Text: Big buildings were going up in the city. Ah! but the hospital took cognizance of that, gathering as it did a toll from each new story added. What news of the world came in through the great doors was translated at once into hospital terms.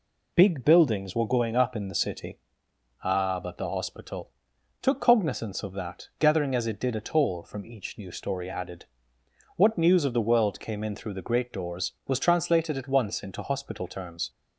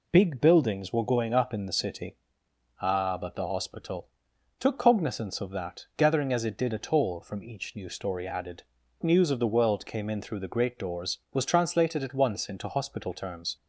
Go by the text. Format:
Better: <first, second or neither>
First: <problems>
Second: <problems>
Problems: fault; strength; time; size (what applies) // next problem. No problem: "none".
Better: first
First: pauses between "hospital" and "took"; noticeable; at 4.2 s; 0.50 s long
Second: pauses between "hospital" and "took"; noticeable; at 4.0 s; 0.50 s long // skips "What"; at 8.8 s